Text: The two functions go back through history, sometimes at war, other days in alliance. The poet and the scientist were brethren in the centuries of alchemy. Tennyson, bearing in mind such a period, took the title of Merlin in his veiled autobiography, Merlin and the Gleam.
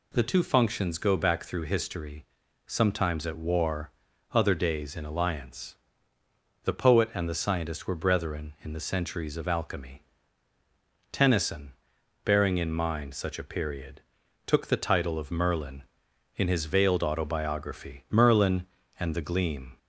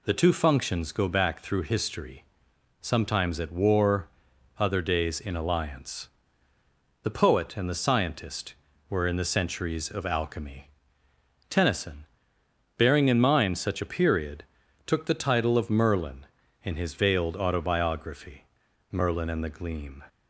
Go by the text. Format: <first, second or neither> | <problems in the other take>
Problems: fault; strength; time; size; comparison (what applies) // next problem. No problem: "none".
first | skips "brethren"; at 9.0 s